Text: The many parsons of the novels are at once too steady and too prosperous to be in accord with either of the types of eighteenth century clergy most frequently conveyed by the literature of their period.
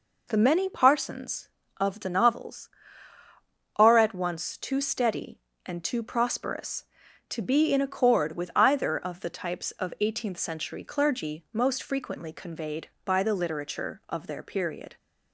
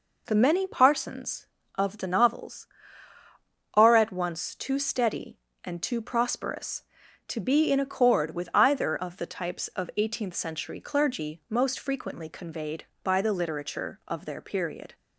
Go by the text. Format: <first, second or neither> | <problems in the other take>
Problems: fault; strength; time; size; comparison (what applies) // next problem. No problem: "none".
neither | none